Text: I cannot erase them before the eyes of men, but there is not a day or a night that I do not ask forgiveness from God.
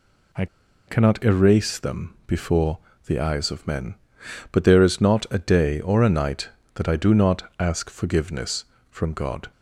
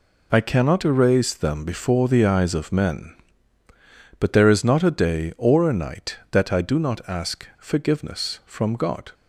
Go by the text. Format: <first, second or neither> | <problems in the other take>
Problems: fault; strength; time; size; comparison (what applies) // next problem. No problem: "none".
second | pauses between "I" and "cannot"; at 0.4 s; 0.41 s long // pauses between "before" and "the"; slight; at 2.7 s; 0.28 s long // pauses between "not" and "ask"; slight; at 7.4 s; 0.16 s long